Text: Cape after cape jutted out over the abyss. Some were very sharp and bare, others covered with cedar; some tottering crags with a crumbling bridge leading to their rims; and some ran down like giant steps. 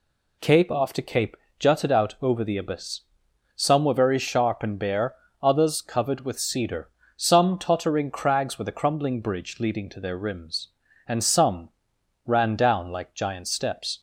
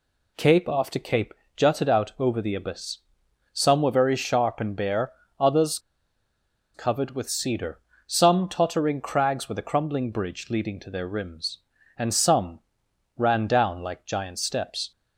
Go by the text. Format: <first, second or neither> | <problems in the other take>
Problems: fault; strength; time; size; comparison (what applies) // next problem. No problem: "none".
first | pauses between "cape" and "jutted"; slight; at 1.3 s; 0.22 s long; slight in the first // pauses between "others" and "covered"; noticeable; at 5.7 s; 0.95 s long // pauses between "some" and "ran"; noticeable; at 12.5 s; 0.58 s long; noticeable in the first